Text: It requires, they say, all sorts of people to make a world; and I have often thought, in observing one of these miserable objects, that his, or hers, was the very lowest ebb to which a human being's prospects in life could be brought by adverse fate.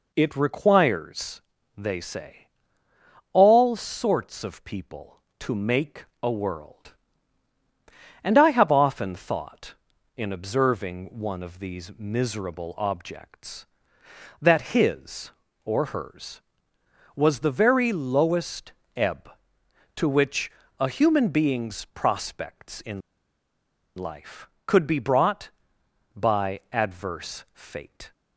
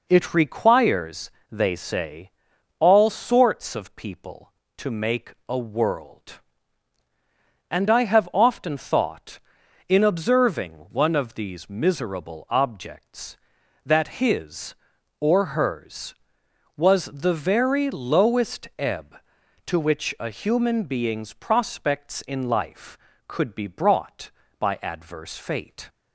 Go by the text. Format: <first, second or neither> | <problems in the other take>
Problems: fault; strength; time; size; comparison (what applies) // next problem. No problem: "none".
second | pauses between "make" and "a"; slight; at 6.0 s; 0.18 s long; slight in the second // pauses between "lowest" and "ebb"; slight; at 18.7 s; 0.22 s long // pauses between "which" and "a"; slight; at 20.5 s; 0.26 s long // pauses between "in" and "life"; noticeable; at 23.0 s; 0.96 s long